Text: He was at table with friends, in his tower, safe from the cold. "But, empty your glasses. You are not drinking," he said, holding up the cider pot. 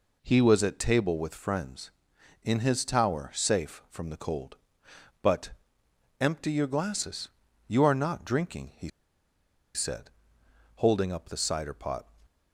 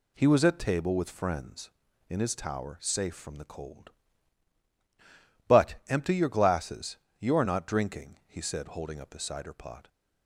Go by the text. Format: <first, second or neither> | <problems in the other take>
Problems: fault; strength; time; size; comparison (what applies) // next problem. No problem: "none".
second | pauses between "he" and "said"; noticeable; at 8.8 s; 0.85 s long